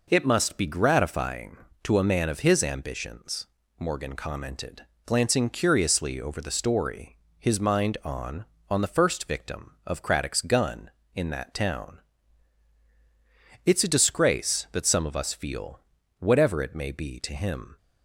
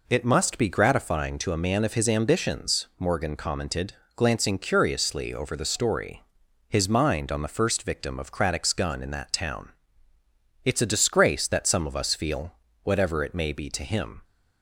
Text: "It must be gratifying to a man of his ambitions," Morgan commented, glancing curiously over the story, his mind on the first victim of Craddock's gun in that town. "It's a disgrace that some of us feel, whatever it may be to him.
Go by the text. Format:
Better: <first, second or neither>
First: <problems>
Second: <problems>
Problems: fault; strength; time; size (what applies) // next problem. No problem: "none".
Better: second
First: says "on" twice; at 8.6 s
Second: none